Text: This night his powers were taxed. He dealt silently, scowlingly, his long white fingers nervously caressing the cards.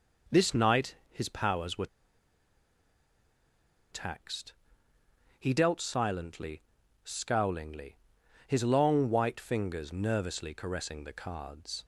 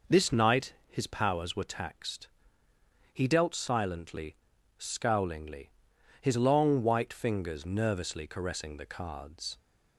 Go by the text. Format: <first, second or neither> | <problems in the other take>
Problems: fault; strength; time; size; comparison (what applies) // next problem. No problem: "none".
second | pauses between "were" and "taxed"; strong; at 1.8 s; 2.0 s long